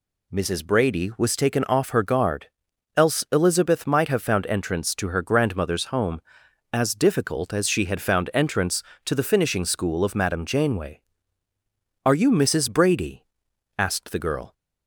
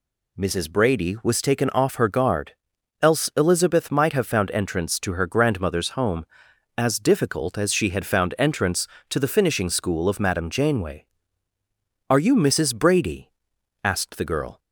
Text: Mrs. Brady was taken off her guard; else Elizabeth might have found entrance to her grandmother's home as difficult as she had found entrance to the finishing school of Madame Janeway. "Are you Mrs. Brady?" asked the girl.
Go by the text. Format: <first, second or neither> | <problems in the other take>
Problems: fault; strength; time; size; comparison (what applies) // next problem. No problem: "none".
neither | none